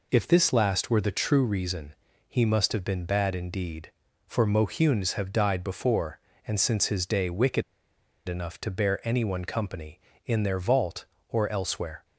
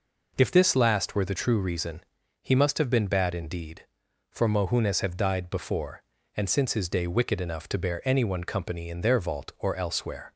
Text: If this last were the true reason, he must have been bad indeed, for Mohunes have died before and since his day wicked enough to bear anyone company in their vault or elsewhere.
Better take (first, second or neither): second